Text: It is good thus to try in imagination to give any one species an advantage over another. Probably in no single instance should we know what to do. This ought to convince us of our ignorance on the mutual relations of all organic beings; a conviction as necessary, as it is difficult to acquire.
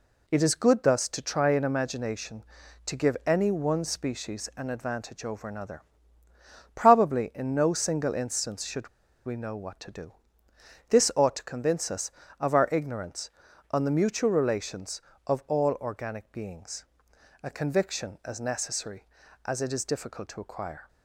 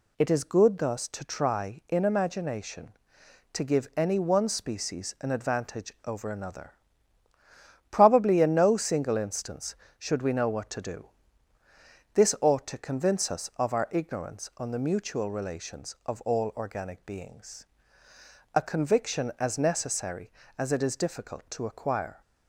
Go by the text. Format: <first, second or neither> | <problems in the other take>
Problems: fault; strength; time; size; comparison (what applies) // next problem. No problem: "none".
second | pauses between "should" and "we"; at 8.8 s; 0.37 s long